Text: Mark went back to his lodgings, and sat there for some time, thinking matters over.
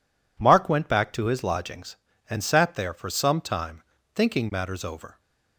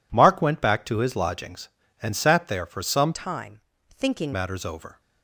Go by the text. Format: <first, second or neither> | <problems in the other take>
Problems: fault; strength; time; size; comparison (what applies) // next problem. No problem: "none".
first | changes voice from "time" to "thinking"; from 3.1 to 4.3 s; 1.2 s long